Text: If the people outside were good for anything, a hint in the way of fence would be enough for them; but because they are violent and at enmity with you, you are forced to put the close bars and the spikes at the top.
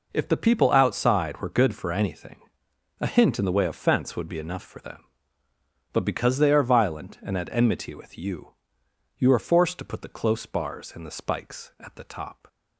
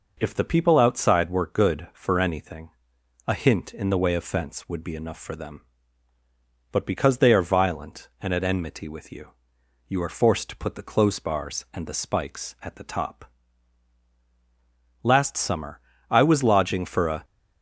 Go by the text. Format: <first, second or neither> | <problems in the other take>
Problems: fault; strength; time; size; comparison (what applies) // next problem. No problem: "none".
first | goes on to say "Last summer I was lodging for a"; strong; from 15.0 s on; 2.2 s long